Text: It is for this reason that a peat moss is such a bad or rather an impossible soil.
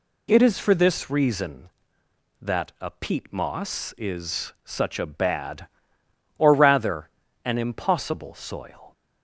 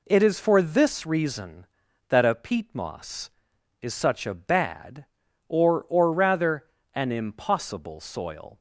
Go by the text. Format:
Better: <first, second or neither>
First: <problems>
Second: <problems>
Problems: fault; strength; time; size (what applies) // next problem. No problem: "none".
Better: first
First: pauses between "rather" and "an"; slight; at 7.0 s; 0.34 s long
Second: says "or" twice; at 5.8 s // pauses between "rather" and "an"; slight; at 6.6 s; 0.28 s long